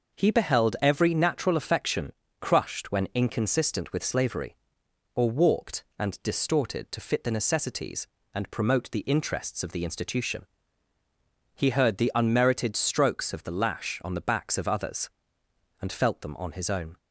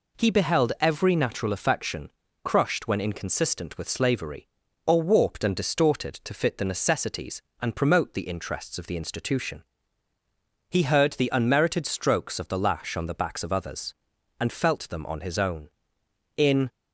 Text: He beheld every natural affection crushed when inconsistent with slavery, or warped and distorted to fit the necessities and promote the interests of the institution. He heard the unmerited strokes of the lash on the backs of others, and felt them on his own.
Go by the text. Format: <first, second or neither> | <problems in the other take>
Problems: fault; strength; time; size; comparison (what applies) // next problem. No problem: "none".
first | pauses between "affection" and "crushed"; slight; at 2.0 s; 0.34 s long; slight in the first // goes on to say "In"; slight; from 16.3 s on; 0.32 s long